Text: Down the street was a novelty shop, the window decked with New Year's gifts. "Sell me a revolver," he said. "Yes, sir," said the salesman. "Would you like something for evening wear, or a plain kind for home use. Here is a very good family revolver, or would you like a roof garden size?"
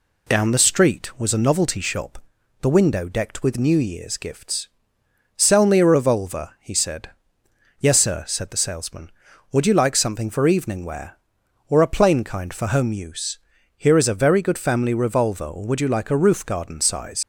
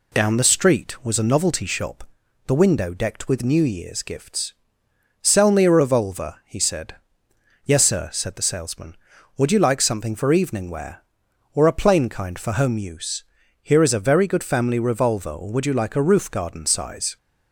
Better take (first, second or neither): second